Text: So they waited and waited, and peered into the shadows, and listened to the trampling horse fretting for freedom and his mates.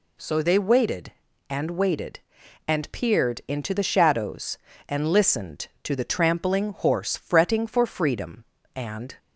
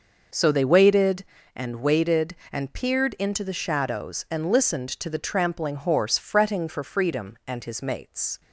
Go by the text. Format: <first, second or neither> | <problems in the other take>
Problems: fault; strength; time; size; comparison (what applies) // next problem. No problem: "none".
second | stops before "his mates"; at 9.1 s